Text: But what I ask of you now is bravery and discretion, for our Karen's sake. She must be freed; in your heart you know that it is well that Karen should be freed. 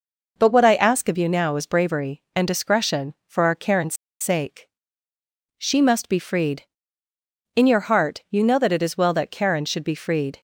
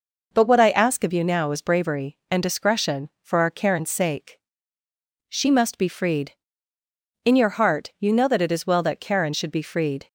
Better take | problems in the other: second | pauses between "Karen's" and "sake"; slight; at 3.9 s; 0.24 s long

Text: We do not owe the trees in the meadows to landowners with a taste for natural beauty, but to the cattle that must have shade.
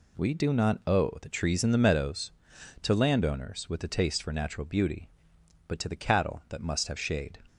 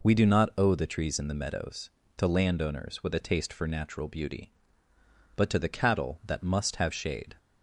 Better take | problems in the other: neither | none

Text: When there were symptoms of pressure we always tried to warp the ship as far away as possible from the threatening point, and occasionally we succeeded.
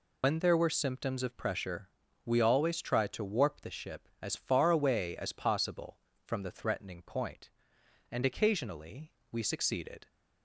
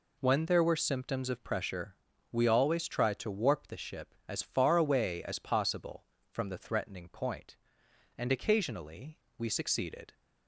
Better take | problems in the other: second | loses the start of "When"; at 0.2 s; 110 ms // pauses between "pressure" and "we"; at 1.8 s; 0.38 s long; also in the second // pauses between "occasionally" and "we"; slight; at 9.1 s; 0.18 s long; slight in the second

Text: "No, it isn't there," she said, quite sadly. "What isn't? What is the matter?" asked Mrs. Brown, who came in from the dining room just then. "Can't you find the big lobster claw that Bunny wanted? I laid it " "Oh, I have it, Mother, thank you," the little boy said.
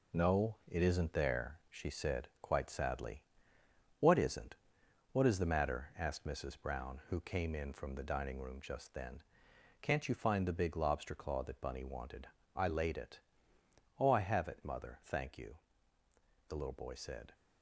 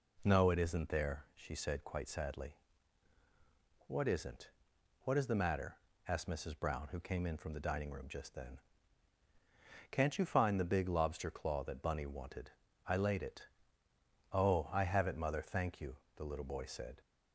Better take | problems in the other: second | gets quieter; strong; throughout; 8.5 dB

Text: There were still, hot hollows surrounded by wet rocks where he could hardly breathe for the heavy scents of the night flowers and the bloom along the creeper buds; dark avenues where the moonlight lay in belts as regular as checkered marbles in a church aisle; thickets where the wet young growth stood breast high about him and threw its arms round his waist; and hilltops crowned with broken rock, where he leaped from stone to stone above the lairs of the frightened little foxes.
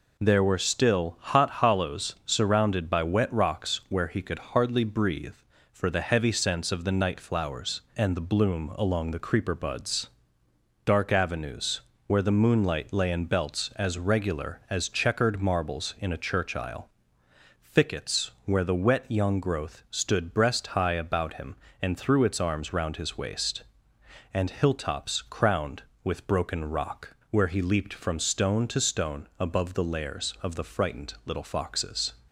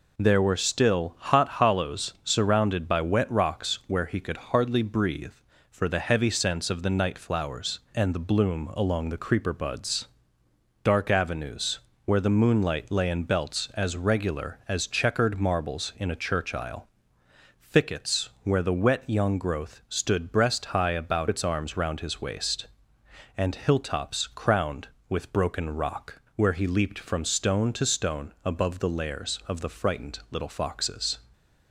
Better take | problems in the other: first | pauses between "avenues" and "where"; slight; at 11.7 s; 0.26 s long; slight in the first // skips "him and threw"; at 21.2 s

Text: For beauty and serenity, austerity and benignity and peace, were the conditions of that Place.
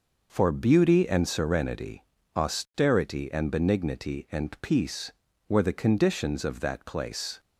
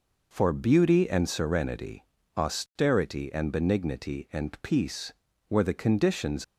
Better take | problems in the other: first | stops before "of that Place"; at 6.4 s

